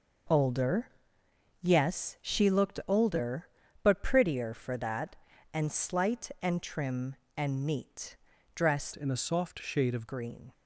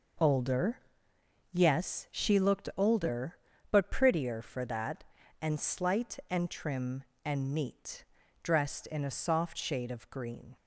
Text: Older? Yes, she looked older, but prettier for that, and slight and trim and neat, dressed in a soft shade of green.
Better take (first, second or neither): second